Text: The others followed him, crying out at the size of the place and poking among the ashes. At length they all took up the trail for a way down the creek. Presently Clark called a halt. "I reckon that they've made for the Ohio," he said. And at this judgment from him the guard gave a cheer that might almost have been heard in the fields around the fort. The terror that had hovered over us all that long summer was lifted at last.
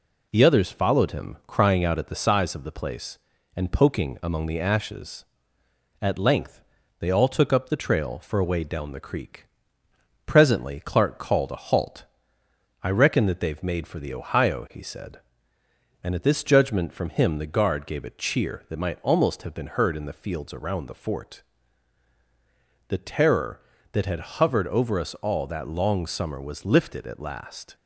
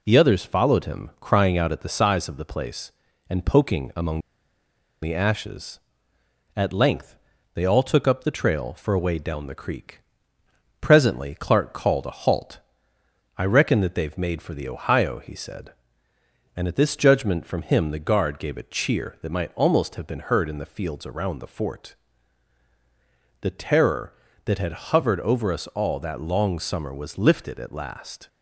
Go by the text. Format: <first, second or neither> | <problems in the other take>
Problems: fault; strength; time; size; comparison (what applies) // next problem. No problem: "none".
first | pauses between "among" and "the"; noticeable; at 4.2 s; 0.81 s long // pauses between "length" and "they"; at 7.1 s; 0.38 s long; also in the first